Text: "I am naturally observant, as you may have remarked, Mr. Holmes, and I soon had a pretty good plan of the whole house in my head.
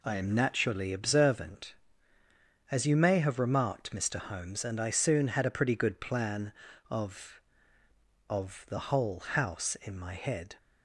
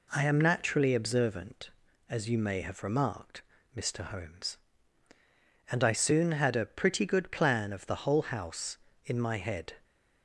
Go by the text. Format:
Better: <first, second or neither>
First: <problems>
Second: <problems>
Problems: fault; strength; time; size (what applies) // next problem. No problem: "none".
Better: second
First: says "of" twice; at 8.2 s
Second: none